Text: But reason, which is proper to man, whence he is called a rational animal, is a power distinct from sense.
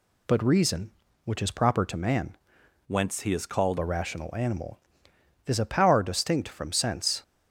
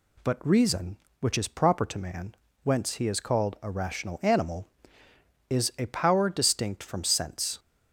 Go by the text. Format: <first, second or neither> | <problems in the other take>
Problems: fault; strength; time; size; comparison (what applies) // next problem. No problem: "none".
second | changes voice from "whence" to "called"; from 2.8 to 3.7 s; 0.9 s long